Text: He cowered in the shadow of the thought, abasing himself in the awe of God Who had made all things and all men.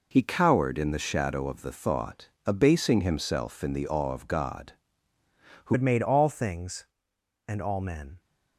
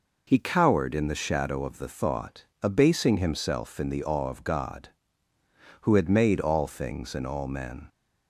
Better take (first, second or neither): second